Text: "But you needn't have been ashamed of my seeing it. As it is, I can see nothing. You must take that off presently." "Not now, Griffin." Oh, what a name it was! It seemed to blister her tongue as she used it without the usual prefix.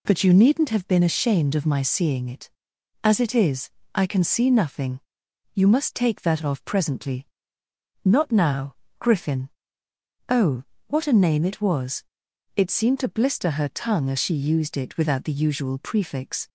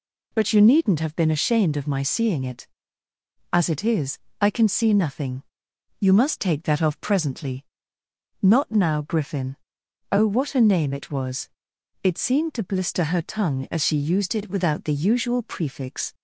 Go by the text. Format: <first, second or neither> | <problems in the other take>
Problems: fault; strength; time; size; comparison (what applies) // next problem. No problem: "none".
neither | none